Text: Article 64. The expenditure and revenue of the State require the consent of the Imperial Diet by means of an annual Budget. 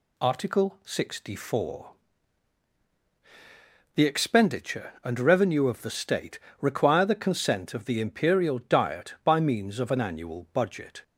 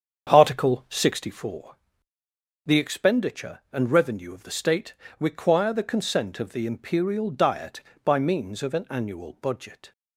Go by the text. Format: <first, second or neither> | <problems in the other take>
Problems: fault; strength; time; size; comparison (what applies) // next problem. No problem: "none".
first | starts louder than the rest; strong; until 1.3 s; 7.5 dB // pauses between "State" and "require"; slight; at 4.9 s; 0.26 s long; slight in the first